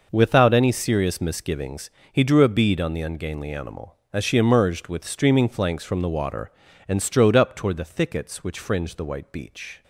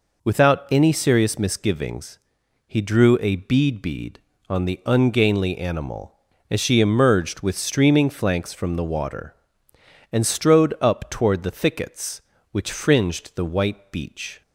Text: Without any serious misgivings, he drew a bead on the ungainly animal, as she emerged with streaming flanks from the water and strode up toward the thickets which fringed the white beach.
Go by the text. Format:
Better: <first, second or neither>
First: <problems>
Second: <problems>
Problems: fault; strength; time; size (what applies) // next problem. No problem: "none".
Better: first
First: none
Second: says "bead" twice; at 3.7 s